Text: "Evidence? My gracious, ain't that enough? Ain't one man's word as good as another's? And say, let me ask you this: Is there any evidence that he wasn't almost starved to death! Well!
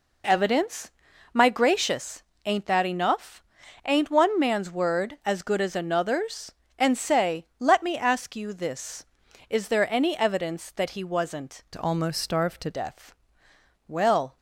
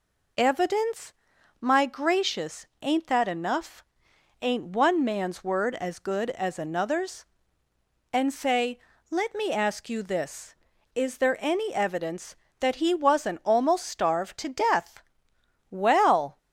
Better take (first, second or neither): second